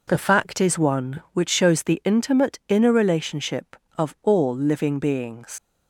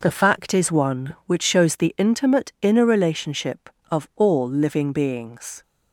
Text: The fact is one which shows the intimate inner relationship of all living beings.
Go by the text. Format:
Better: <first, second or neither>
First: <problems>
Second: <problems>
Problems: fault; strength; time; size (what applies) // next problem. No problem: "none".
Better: second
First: leaves "beings" unfinished; at 5.5 s; 105 ms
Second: none